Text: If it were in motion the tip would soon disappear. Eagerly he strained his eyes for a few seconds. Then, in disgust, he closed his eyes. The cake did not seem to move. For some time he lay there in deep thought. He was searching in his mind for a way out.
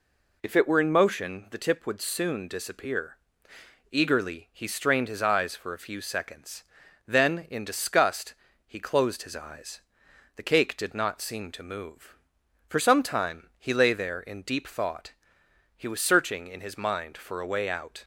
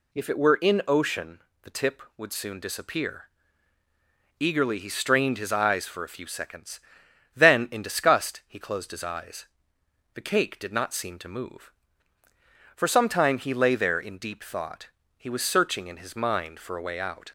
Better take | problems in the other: first | says "ocean" for "motion"; at 0.8 s

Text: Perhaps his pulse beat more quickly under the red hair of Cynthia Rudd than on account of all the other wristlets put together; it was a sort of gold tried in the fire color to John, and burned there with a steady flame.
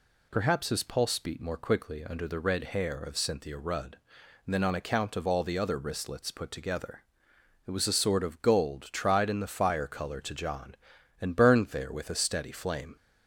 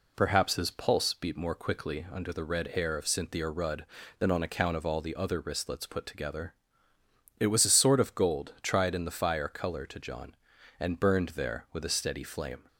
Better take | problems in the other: neither | none

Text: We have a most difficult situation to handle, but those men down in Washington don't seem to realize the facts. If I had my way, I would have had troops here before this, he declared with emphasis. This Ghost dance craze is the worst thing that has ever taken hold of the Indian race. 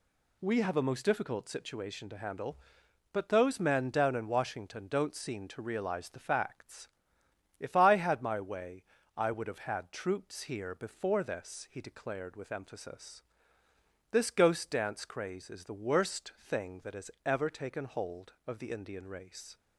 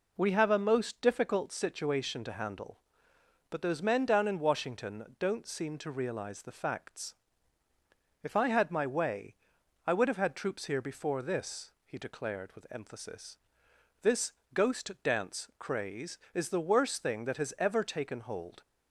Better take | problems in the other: first | pauses between "Washington" and "don't"; slight; at 5.0 s; 0.16 s long // pauses between "This" and "Ghost"; slight; at 14.3 s; 0.22 s long // stops before "of the Indian race"; at 18.6 s

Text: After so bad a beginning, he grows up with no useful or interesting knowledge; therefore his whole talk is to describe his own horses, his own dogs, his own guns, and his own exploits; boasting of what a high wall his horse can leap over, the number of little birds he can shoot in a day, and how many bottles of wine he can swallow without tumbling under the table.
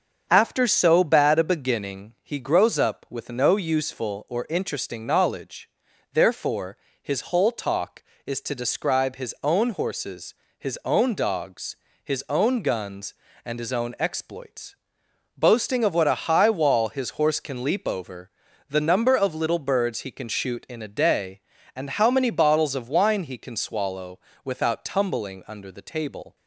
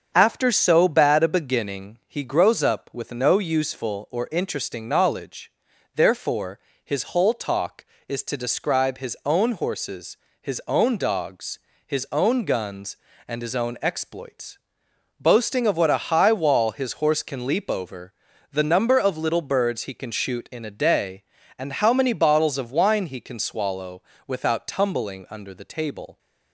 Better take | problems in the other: neither | starts louder than the rest; the same in both // pauses between "therefore" and "his"; slight; the same in both // pauses between "swallow" and "without"; slight; the same in both

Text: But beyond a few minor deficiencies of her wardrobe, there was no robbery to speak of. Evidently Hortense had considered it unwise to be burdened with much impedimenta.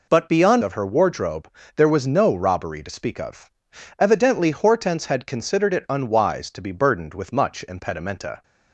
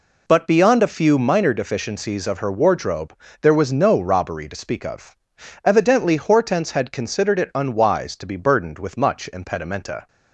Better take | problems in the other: second | skips "a few minor deficiencies"; at 0.6 s

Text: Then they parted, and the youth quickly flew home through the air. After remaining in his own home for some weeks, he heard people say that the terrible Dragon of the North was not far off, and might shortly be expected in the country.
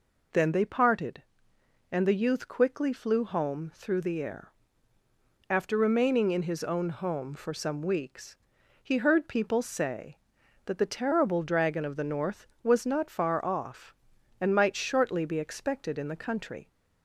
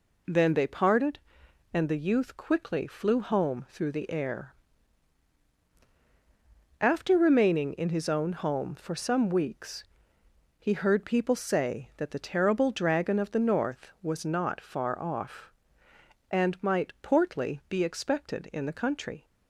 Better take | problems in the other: first | says "portly" for "shortly"; at 17.0 s

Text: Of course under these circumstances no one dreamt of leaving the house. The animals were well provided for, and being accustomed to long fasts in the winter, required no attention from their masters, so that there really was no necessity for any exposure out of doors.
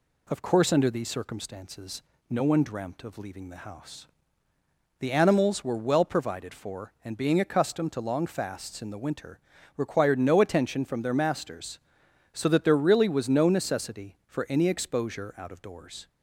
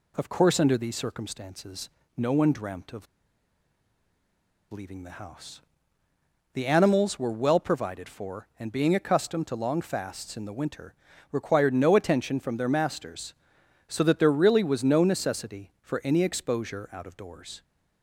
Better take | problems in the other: first | pauses between "circumstances" and "no"; slight; at 1.8 s; 0.28 s long; slight in the first // pauses between "of" and "leaving"; strong; at 3.0 s; 1.6 s long

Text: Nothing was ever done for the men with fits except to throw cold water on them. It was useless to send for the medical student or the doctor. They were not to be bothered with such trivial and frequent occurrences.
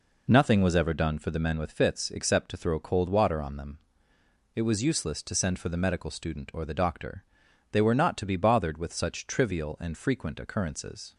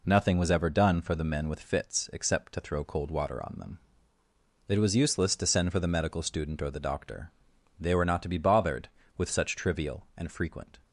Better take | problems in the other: first | stops before "occurrences"; at 10.8 s

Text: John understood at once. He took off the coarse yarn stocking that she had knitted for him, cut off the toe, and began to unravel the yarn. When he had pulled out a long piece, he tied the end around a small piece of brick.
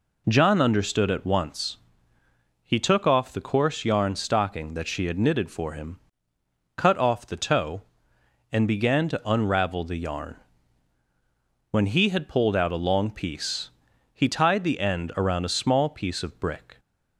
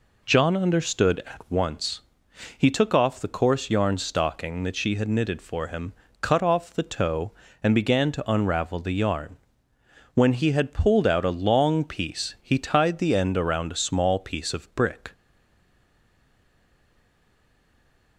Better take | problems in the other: first | stays silent after the last word; strong; from 15.1 s on; 3.0 s long

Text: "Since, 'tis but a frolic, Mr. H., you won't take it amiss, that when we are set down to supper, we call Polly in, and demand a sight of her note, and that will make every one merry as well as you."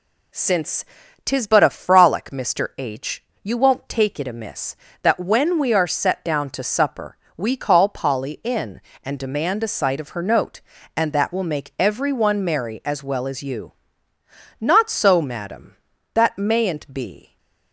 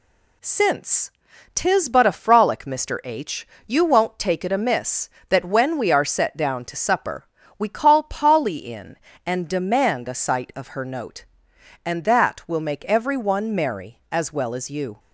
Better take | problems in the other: second | goes on to say "Not so Madam that mayn't be"; strong; from 14.6 s on; 2.7 s long

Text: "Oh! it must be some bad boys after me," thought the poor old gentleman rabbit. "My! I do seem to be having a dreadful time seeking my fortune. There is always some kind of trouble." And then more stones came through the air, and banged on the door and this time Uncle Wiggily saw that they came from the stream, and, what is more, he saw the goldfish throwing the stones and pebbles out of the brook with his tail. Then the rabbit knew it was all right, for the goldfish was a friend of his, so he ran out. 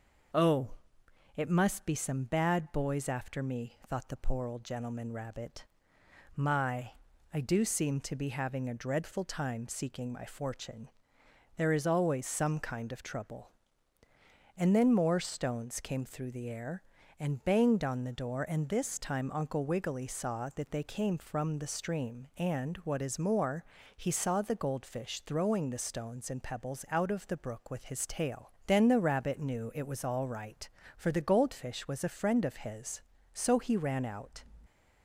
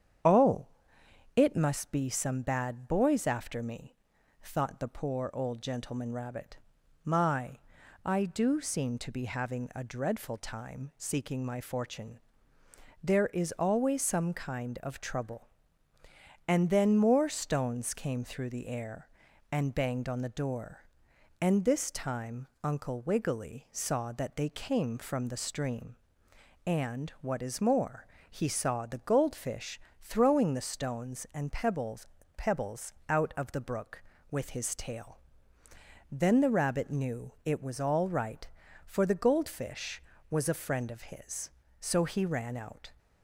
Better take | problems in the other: first | starts louder than the rest; strong; until 1.9 s; 8.5 dB; noticeable in the first // pauses between "time" and "Uncle"; slight; at 22.4 s; 0.16 s long // pauses between "goldfish" and "throwing"; slight; at 29.7 s; 0.22 s long // says "pebbles" twice; at 32.3 s

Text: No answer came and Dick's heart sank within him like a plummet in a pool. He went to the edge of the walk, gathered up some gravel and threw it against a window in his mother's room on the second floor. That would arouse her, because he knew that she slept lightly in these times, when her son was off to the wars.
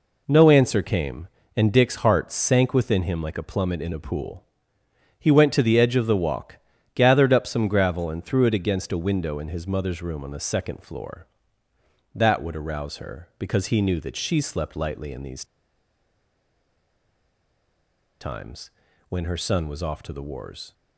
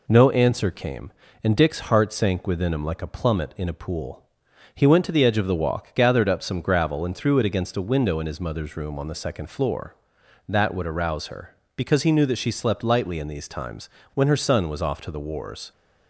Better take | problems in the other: second | pauses between "these" and "times"; strong; at 15.4 s; 2.7 s long

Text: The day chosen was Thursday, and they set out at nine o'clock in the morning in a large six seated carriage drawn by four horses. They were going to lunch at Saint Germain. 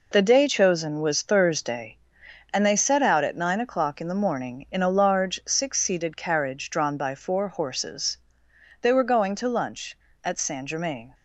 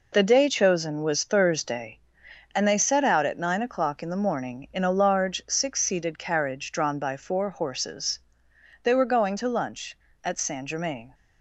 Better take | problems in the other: neither | none

